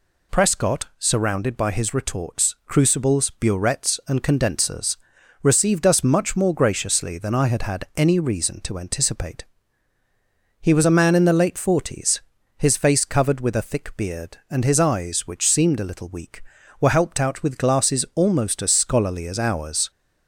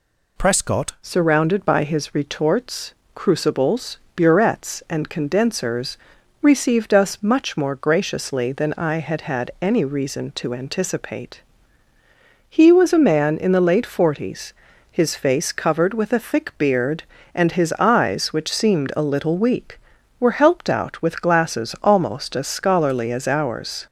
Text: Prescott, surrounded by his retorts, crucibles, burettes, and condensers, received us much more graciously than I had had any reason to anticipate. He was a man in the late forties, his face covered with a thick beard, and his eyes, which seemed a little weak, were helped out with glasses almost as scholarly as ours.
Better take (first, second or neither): first